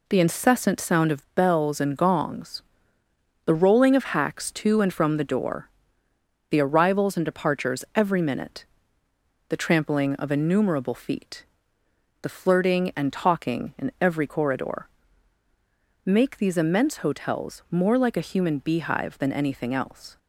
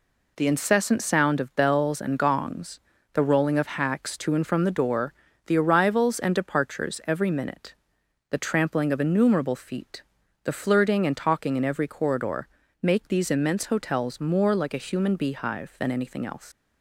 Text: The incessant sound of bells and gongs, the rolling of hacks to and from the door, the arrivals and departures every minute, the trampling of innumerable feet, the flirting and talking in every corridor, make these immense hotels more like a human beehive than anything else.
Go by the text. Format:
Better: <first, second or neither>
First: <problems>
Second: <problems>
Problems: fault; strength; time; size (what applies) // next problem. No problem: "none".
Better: first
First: none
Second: leaves "else" unfinished; at 16.5 s; 110 ms